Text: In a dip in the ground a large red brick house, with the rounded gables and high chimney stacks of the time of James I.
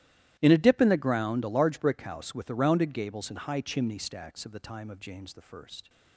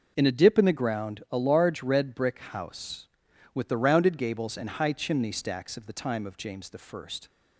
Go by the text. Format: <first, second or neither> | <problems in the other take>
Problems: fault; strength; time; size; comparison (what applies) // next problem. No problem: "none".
second | starts louder than the rest; strong; until 1.4 s; 14 dB // skips "red"; at 1.7 s